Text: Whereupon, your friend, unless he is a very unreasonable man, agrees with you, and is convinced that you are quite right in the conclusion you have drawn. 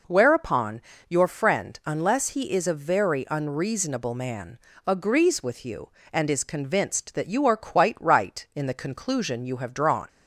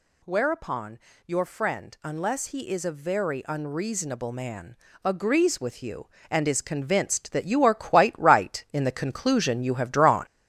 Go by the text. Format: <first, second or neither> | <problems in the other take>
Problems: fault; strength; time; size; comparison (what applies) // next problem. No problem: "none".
first | gets louder; noticeable; throughout; 5.5 dB